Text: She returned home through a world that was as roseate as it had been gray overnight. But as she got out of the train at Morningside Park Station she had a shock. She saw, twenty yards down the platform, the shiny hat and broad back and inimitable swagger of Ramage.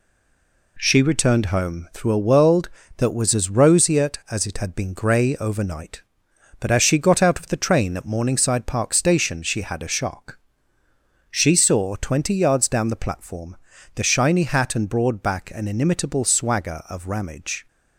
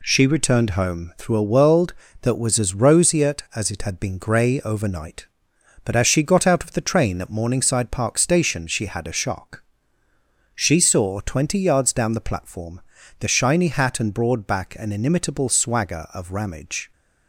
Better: second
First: stays silent before the first word; slight; until 0.7 s; 0.7 s long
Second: none

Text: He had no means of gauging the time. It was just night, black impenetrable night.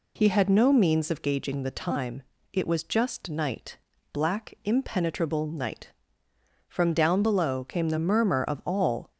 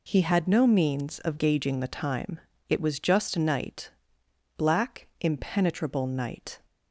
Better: second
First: goes on to say "From down below came the murmur of all"; strong; from 6.7 s on; 2.4 s long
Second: none

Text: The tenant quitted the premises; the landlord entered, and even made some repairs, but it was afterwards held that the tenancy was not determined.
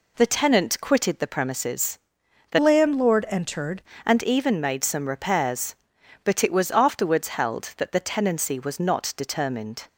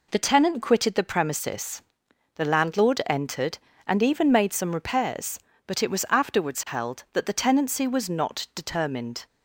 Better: second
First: changes voice from "landlord" to "entered"; from 2.5 to 3.8 s; 1.3 s long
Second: none

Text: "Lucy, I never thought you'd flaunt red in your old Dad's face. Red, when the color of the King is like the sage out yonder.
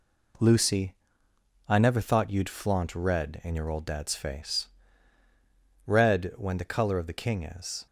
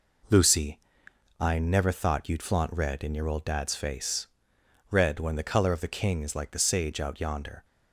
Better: second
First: stops before "like the sage out yonder"; at 7.8 s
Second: none

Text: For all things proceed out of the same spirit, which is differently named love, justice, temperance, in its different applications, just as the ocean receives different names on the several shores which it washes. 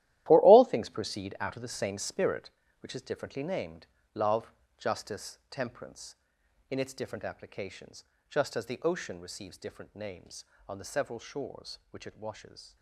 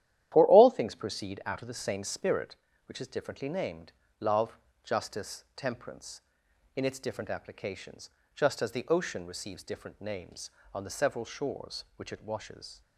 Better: second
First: gets quieter; strong; throughout; 12 dB // starts louder than the rest; strong; until 1.2 s; 14 dB // pauses between "named" and "love"; slight; at 3.8 s; 0.26 s long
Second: starts louder than the rest; strong; until 1.3 s; 12 dB // pauses between "named" and "love"; slight; at 3.9 s; 0.26 s long

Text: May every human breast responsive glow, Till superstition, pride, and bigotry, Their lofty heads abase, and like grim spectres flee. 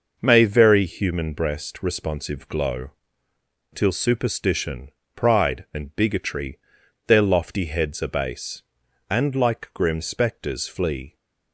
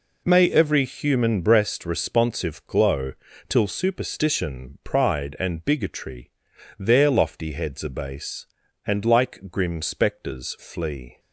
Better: second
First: says "very" for "every"; at 0.4 s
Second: none

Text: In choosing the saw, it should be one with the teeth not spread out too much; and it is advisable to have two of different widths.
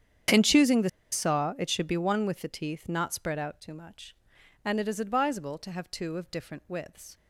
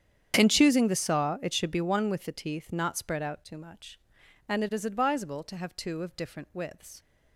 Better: second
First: starts louder than the rest; strong; until 1.5 s; 8.5 dB // pauses between "the" and "saw"; slight; at 0.8 s; 0.23 s long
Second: starts louder than the rest; strong; until 1.3 s; 9 dB

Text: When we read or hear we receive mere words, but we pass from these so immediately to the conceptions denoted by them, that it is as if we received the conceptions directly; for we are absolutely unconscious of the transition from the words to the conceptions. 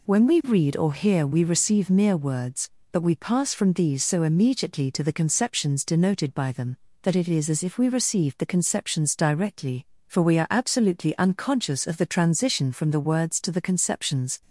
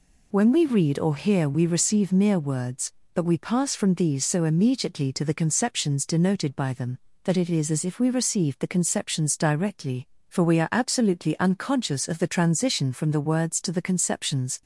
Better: neither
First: none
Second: none

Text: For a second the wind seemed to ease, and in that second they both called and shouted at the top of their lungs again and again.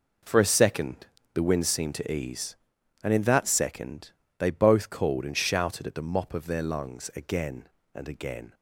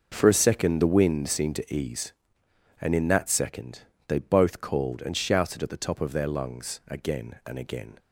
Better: second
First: pauses between "second" and "the"; slight; at 1.0 s; 0.28 s long // pauses between "second" and "they"; slight; at 4.1 s; 0.26 s long // says "mop" for "top"; at 6.0 s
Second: pauses between "second" and "they"; slight; at 3.8 s; 0.26 s long

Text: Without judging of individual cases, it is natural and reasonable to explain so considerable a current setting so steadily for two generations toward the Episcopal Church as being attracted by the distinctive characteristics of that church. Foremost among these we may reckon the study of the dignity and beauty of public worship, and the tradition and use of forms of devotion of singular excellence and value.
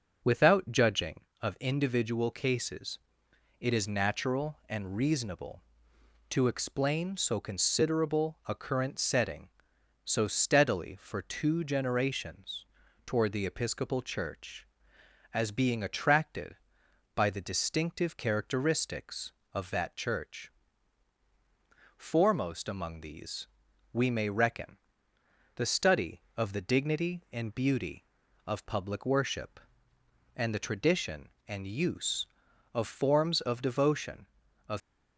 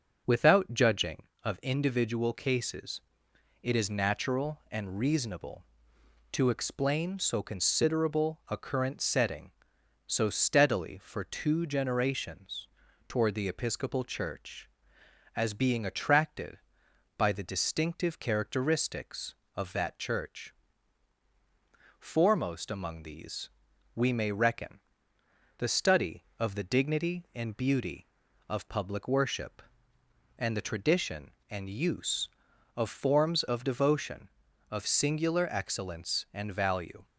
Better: second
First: starts louder than the rest; until 1.4 s; 6.5 dB // pauses between "generations" and "toward"; at 12.6 s; 0.40 s long // pauses between "these" and "we"; noticeable; at 23.4 s; 0.46 s long // pauses between "reckon" and "the"; noticeable; at 24.7 s; 0.80 s long // stops before "singular excellence and value"; at 34.8 s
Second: starts louder than the rest; strong; until 1.4 s; 7 dB // pauses between "generations" and "toward"; at 12.6 s; 0.40 s long // pauses between "these" and "we"; noticeable; at 23.4 s; 0.46 s long // pauses between "reckon" and "the"; noticeable; at 24.7 s; 0.80 s long

